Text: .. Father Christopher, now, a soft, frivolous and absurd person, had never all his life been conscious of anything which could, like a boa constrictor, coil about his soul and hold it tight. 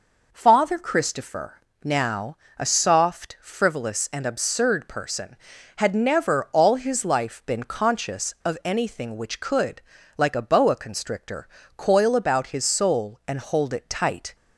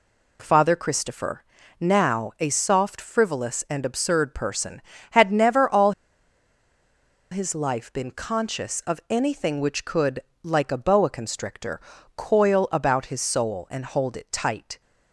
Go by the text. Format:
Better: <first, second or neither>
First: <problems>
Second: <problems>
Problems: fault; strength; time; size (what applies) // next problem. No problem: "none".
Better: first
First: none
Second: pauses between "all" and "his"; strong; at 5.9 s; 1.4 s long